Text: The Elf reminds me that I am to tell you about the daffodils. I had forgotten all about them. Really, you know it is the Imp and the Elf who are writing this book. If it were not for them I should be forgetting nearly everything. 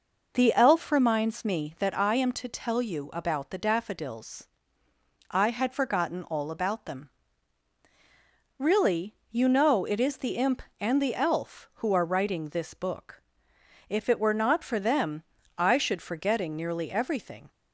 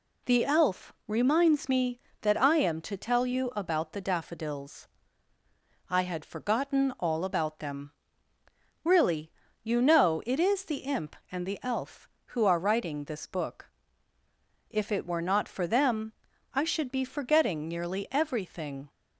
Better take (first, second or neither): second